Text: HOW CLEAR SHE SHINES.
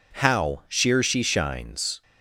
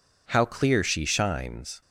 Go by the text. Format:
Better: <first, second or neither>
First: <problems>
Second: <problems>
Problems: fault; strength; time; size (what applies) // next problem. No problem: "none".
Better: second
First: says "Sheer" for "CLEAR"; at 0.6 s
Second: none